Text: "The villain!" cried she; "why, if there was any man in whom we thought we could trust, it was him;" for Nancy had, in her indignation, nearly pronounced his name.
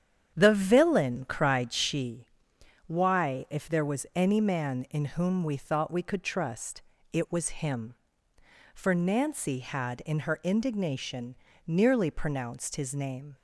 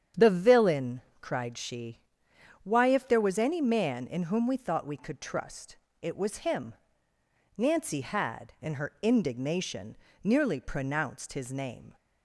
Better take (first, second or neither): first